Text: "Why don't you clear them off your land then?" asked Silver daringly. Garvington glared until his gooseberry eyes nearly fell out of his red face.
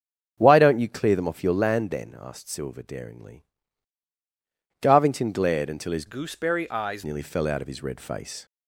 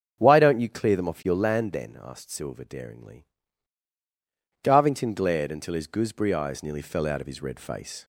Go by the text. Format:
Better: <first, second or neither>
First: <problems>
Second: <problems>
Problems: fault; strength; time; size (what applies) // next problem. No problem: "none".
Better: second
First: starts louder than the rest; until 1.3 s; 7 dB // changes voice from "gooseberry" to "eyes"; from 6.0 to 7.0 s; 1.0 s long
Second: starts louder than the rest; until 1.1 s; 7 dB